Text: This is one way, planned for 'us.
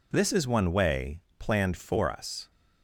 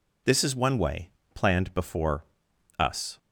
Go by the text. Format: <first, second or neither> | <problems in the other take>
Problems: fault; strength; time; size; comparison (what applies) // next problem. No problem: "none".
first | says "before" for "for"; at 1.7 s